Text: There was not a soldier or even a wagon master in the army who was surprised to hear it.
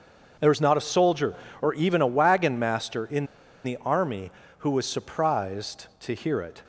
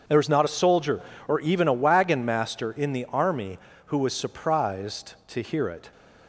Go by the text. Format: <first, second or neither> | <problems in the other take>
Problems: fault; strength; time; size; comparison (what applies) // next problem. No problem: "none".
second | starts louder than the rest; until 1.6 s; 6.5 dB; also in the second // pauses between "in" and "the"; at 3.2 s; 0.38 s long